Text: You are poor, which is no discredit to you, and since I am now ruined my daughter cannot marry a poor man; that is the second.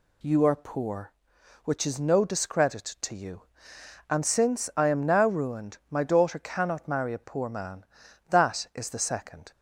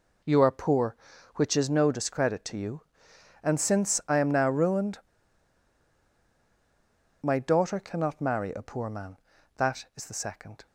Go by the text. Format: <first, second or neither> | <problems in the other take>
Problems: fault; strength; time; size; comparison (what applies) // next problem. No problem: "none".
first | pauses between "ruined" and "my"; strong; at 4.9 s; 2.2 s long